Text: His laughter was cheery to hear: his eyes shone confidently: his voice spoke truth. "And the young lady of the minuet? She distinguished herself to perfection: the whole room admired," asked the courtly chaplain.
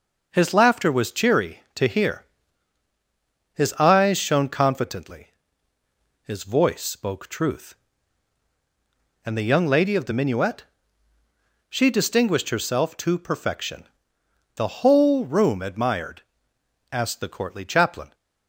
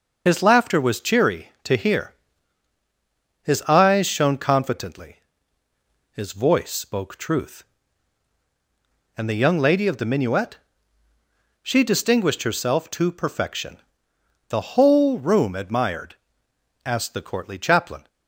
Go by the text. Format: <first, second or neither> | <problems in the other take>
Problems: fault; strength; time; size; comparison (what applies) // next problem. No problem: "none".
first | loses the start of "His"; at 0.2 s; 55 ms // starts louder than the rest; noticeable; until 1.2 s; 6 dB